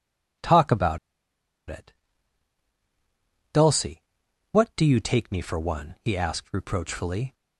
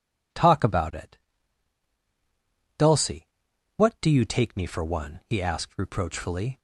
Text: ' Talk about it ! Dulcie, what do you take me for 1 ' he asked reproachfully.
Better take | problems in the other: second | pauses between "about" and "it"; noticeable; at 0.9 s; 0.70 s long

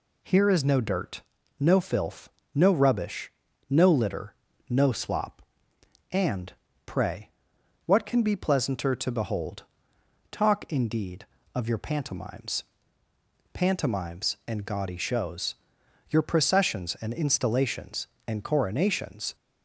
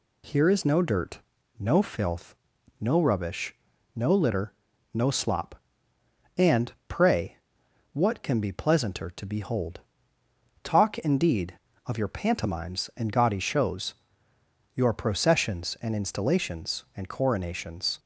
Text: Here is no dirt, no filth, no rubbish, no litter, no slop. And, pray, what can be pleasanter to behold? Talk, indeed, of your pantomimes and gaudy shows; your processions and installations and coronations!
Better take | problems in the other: second | says "pantomimes" twice; at 13.5 s

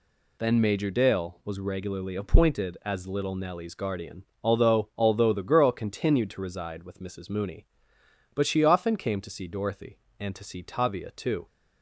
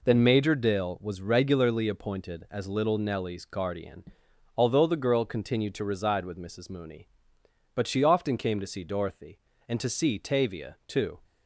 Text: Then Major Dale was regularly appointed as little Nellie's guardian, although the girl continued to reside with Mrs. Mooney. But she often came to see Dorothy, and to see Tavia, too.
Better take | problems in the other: second | says "although" twice; at 4.9 s

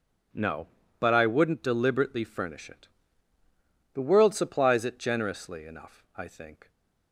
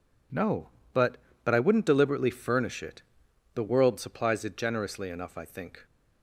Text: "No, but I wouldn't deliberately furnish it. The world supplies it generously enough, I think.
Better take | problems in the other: first | says "but" twice; at 1.4 s

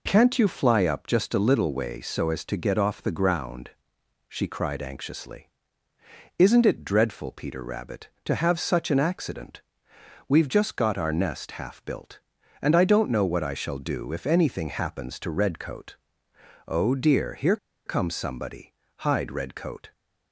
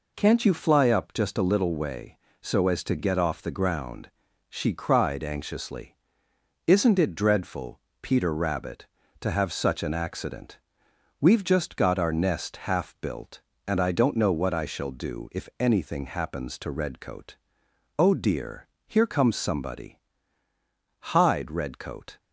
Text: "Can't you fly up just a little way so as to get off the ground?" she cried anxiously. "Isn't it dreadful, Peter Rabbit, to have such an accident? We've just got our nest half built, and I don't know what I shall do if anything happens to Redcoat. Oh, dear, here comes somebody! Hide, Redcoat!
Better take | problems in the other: second | pauses between "here" and "comes"; slight; at 17.5 s; 0.29 s long

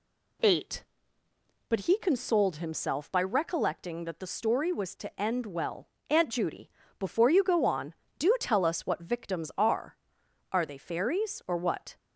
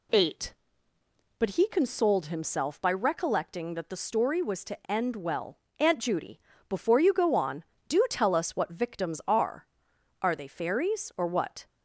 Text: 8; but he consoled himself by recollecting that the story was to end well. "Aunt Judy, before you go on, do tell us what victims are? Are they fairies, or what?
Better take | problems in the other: neither | none

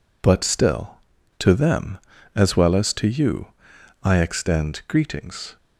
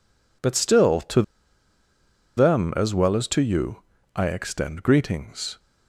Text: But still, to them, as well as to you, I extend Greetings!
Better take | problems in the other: first | pauses between "to" and "them"; at 1.2 s; 1.1 s long

